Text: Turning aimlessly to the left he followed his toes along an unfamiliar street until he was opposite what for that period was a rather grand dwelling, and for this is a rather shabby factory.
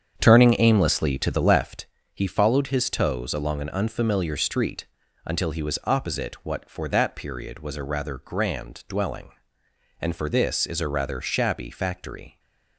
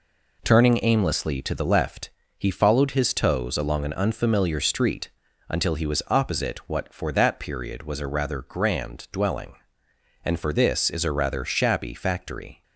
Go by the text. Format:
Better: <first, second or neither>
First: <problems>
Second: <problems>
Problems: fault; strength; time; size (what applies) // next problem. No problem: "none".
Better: second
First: starts louder than the rest; strong; until 1.8 s; 8 dB // pauses between "left" and "he"; slight; at 1.8 s; 0.28 s long // pauses between "street" and "until"; at 4.8 s; 0.38 s long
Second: pauses between "left" and "he"; slight; at 2.1 s; 0.28 s long // pauses between "street" and "until"; at 5.1 s; 0.38 s long